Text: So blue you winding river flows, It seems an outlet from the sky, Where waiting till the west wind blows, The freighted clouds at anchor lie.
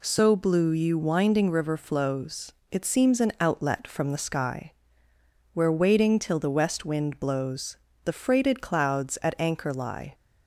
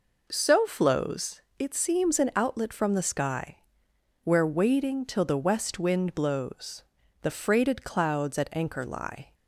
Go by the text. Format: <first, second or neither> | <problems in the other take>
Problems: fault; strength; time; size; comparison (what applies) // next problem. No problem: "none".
first | skips "blue you winding river"; at 0.6 s